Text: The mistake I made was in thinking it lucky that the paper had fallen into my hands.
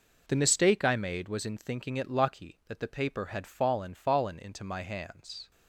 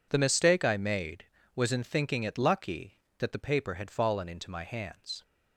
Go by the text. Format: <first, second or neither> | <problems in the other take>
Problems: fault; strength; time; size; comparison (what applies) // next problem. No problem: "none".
second | says "fallen" twice; at 3.9 s